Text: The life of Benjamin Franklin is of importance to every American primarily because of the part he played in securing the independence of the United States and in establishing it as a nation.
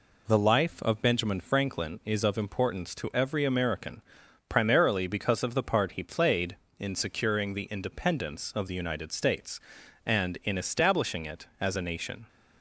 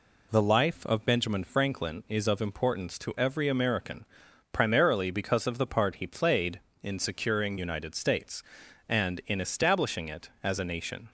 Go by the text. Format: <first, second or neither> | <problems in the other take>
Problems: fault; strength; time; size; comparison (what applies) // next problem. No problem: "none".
first | pauses between "American" and "primarily"; noticeable; at 4.0 s; 0.46 s long; noticeable in the first // skips "the independence of the"; at 7.5 s